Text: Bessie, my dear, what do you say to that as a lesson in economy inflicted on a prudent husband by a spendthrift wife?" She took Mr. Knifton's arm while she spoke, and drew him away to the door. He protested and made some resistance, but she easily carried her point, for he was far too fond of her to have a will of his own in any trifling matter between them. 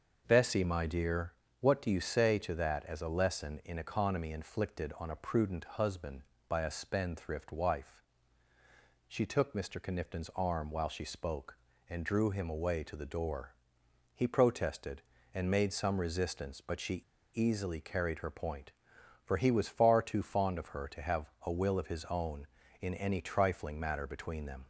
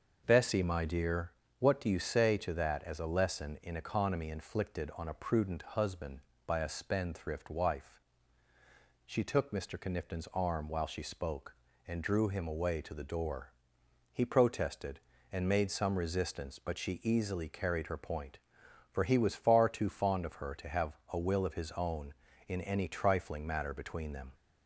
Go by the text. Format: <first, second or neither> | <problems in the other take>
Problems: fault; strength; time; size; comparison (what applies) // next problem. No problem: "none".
second | starts louder than the rest; until 1.2 s; 6 dB; also in the second // pauses between "she" and "easily"; slight; at 17.0 s; 0.31 s long // pauses between "have" and "a"; slight; at 21.2 s; 0.16 s long; slight in the second